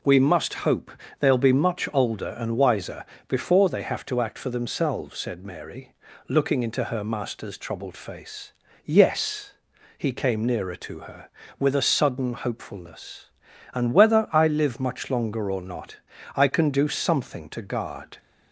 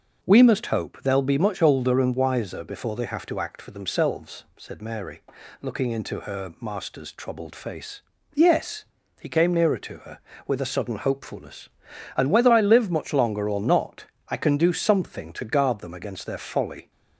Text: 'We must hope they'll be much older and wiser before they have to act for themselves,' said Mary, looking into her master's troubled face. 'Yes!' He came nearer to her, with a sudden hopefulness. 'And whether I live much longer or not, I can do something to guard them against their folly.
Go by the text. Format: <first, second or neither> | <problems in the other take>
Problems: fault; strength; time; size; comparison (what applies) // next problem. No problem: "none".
second | pauses between "hope" and "they'll"; slight; at 0.9 s; 0.28 s long // pauses between "wiser" and "before"; slight; at 3.0 s; 0.24 s long // stops before "them against their folly"; at 18.1 s